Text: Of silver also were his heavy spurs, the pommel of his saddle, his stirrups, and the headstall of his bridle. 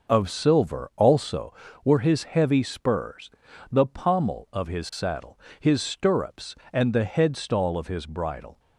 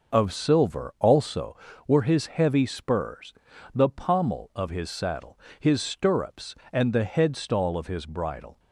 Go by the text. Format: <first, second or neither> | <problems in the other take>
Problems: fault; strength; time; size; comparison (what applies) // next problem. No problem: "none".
neither | starts louder than the rest; noticeable; the same in both